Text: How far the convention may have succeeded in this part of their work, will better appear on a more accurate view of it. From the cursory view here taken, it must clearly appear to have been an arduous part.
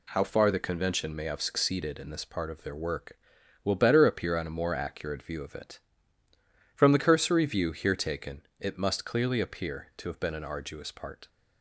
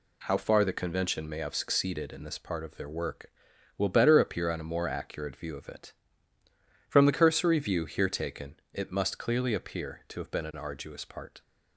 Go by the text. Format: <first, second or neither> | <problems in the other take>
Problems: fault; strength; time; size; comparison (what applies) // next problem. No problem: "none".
neither | none